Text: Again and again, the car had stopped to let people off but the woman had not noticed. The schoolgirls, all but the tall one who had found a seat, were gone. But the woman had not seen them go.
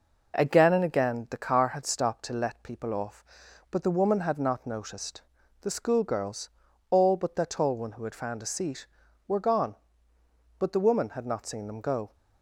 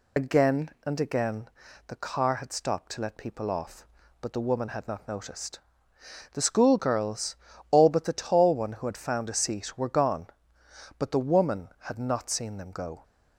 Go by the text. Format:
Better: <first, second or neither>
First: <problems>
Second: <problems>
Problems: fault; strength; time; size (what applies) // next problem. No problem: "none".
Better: first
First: none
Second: loses the start of "Again"; at 0.1 s; 65 ms